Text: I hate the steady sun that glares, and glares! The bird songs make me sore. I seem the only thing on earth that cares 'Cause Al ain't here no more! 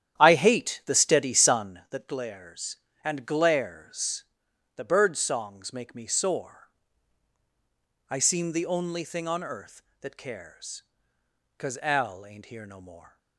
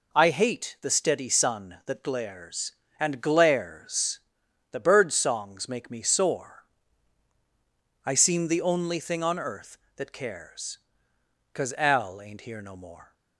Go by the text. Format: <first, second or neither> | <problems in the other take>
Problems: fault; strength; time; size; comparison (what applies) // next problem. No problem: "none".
second | starts louder than the rest; strong; until 1.8 s; 10.5 dB // pauses between "cares" and "Cause"; noticeable; at 10.8 s; 0.74 s long; noticeable in the second